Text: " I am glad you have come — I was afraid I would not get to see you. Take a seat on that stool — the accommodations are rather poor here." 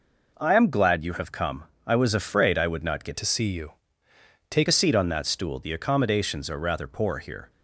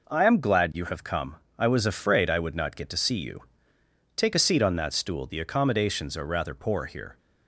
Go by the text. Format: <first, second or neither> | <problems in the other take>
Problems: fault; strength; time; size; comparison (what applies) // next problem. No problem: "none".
second | changes voice from "to" to "Take"; from 3.1 to 4.6 s; 1.5 s long